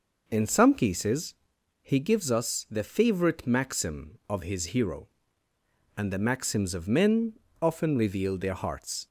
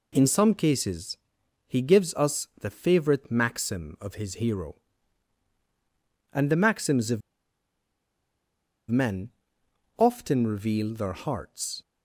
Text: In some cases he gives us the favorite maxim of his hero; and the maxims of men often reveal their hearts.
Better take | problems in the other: first | pauses between "cases" and "he"; noticeable; at 1.1 s; 0.48 s long; noticeable in the first // pauses between "of" and "men"; strong; at 7.2 s; 1.7 s long // pauses between "men" and "often"; noticeable; at 9.3 s; 0.66 s long; slight in the first

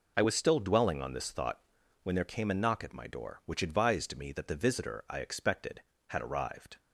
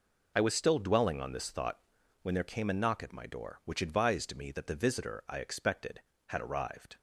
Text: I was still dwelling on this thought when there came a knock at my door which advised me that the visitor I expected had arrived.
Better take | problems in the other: neither | pauses between "thought" and "when"; the same in both

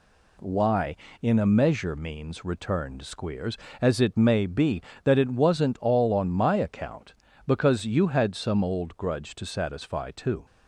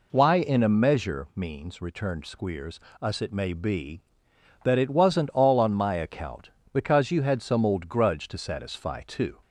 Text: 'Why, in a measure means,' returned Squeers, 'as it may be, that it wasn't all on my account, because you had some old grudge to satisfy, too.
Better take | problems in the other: first | says "us" for "as"; at 2.9 s

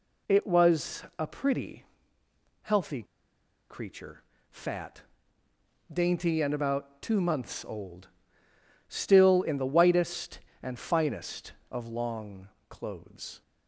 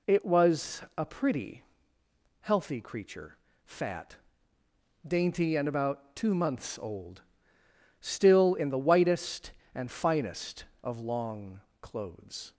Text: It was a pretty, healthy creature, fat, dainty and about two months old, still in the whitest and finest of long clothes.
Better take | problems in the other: second | pauses between "was" and "a"; slight; at 1.0 s; 0.16 s long; slight in the second // pauses between "healthy" and "creature"; noticeable; at 3.0 s; 0.66 s long // pauses between "long" and "clothes"; slight; at 12.4 s; 0.22 s long; slight in the second

